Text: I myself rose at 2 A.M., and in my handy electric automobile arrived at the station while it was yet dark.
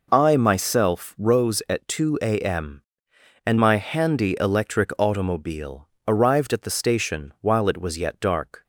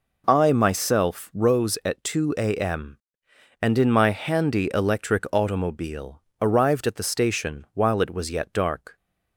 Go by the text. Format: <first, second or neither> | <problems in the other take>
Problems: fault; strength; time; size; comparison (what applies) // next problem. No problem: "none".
second | skips "in"; at 3.5 s // pauses between "automobile" and "arrived"; slight; at 5.8 s; 0.18 s long; slight in the second